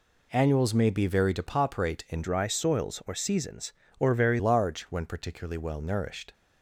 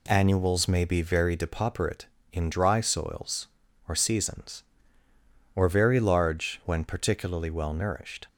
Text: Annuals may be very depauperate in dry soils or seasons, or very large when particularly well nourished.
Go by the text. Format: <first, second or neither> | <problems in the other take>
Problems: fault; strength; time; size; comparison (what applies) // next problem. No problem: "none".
second | changes voice from "dry" to "very"; from 2.2 to 4.3 s; 2.1 s long